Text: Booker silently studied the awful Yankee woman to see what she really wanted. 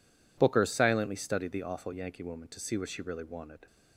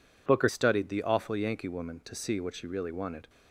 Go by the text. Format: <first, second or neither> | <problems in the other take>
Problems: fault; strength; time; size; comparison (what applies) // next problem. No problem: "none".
first | skips "silently"; at 0.4 s